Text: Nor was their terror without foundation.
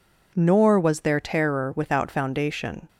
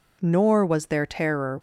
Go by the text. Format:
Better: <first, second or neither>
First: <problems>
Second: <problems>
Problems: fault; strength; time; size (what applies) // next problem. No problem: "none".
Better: first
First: none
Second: stops before "without foundation"; at 1.5 s